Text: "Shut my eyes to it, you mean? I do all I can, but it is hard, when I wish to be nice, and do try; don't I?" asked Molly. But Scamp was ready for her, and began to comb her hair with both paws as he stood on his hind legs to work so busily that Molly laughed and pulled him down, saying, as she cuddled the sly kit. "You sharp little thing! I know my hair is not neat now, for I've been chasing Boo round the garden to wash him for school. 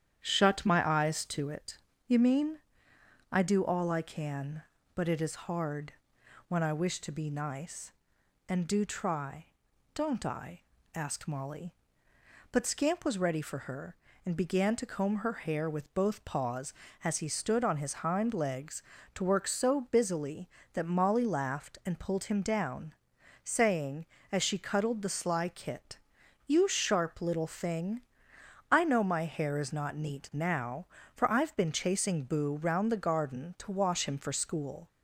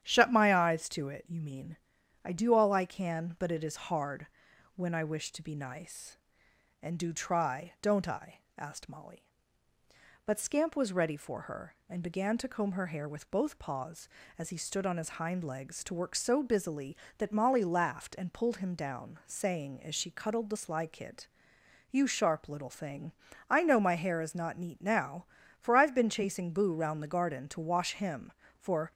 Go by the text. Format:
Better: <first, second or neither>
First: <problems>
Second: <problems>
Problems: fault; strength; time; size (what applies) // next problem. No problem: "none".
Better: first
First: starts louder than the rest; strong; until 1.2 s; 9.5 dB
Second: starts louder than the rest; strong; until 1.0 s; 10 dB // stops before "school"; at 28.9 s